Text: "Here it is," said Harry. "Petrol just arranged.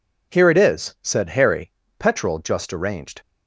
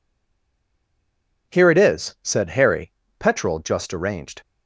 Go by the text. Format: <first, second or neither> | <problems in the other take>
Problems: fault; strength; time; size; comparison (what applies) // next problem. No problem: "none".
first | stays silent before the first word; noticeable; until 1.5 s; 1.5 s long